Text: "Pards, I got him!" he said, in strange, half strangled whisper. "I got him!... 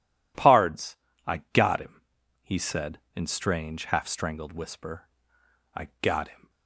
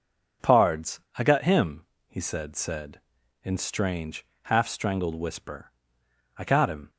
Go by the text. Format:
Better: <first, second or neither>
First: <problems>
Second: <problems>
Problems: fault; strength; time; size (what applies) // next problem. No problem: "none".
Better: first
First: none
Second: says "said" twice; at 2.5 s